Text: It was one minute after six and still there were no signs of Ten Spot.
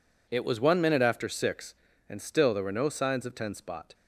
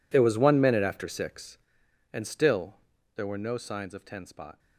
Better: first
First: none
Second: gets quieter; strong; throughout; 19 dB // pauses between "still" and "there"; at 2.7 s; 0.42 s long

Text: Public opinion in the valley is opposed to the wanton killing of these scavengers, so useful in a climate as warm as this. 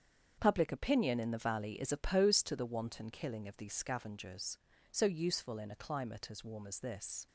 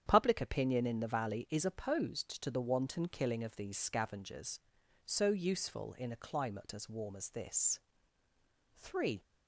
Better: first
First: starts louder than the rest; strong; until 1.3 s; 7.5 dB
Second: starts louder than the rest; strong; until 1.0 s; 9 dB // goes on to say "Three"; slight; from 8.7 s on; 0.44 s long

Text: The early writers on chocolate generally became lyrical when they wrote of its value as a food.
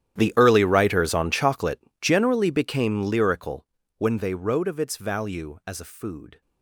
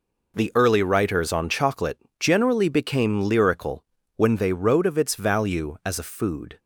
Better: second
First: gets quieter; strong; throughout; 21.5 dB // pauses between "chocolate" and "generally"; slight; at 1.7 s; 0.22 s long // pauses between "lyrical" and "when"; slight; at 3.6 s; 0.32 s long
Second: pauses between "chocolate" and "generally"; slight; at 1.9 s; 0.22 s long // pauses between "lyrical" and "when"; slight; at 3.8 s; 0.32 s long

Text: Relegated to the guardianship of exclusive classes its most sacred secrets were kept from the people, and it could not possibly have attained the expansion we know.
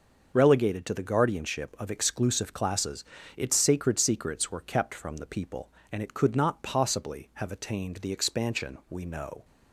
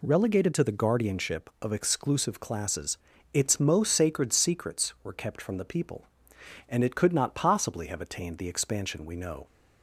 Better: second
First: starts louder than the rest; noticeable; until 1.3 s; 6 dB // pauses between "classes" and "its"; slight; at 3.0 s; 0.32 s long // skips "most"; at 3.5 s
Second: pauses between "classes" and "its"; slight; at 2.9 s; 0.36 s long

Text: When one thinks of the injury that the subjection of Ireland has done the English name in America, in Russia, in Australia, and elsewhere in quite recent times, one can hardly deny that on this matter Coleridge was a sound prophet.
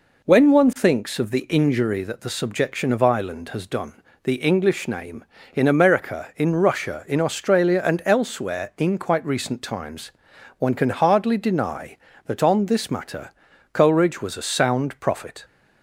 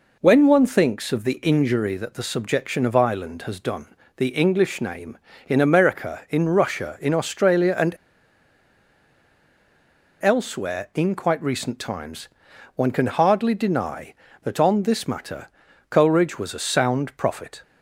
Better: first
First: pauses between "done" and "the"; slight; at 4.0 s; 0.22 s long // pauses between "matter" and "Coleridge"; noticeable; at 13.2 s; 0.46 s long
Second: pauses between "done" and "the"; slight; at 3.9 s; 0.22 s long // pauses between "and" and "elsewhere"; strong; at 7.9 s; 2.2 s long // pauses between "matter" and "Coleridge"; noticeable; at 15.4 s; 0.46 s long

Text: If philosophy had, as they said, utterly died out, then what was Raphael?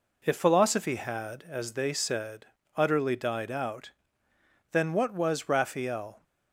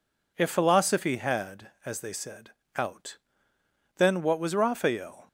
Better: first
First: none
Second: skips "utterly died"; at 2.6 s

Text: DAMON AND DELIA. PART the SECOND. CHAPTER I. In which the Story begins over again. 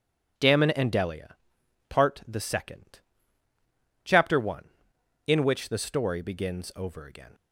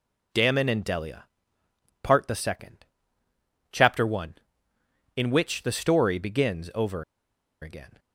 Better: first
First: none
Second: pauses between "over" and "again"; noticeable; at 7.0 s; 0.58 s long

